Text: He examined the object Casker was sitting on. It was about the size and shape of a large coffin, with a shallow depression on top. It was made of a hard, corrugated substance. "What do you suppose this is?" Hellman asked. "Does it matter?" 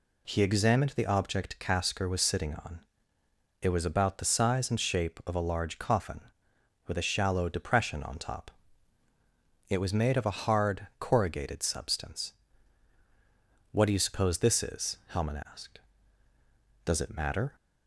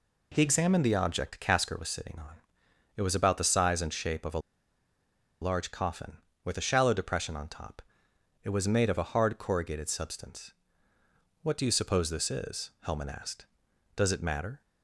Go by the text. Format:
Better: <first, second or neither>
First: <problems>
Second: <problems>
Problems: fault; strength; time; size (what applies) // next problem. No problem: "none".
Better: first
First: none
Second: pauses between "a" and "large"; at 4.3 s; 1.0 s long